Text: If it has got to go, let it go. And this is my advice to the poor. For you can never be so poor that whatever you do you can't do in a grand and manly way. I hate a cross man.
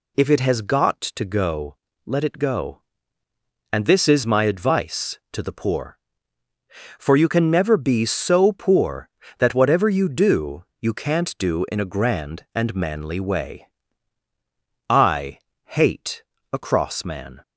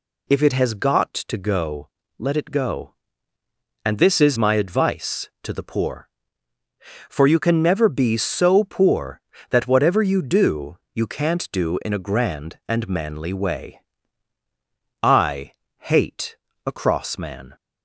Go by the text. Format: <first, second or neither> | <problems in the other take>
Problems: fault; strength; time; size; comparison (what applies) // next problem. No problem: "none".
neither | pauses between "do" and "you"; slight; the same in both // pauses between "I" and "hate"; slight; the same in both // pauses between "hate" and "a"; slight; the same in both